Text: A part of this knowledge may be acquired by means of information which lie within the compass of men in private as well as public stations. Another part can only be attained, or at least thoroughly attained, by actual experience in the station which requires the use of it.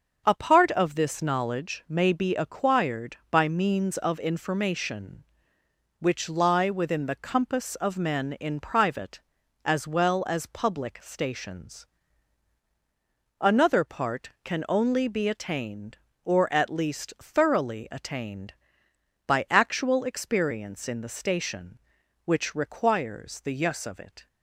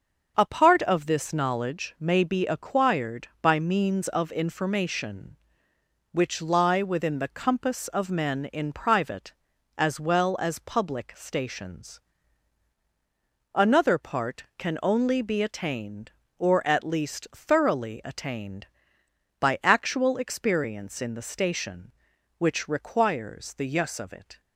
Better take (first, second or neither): neither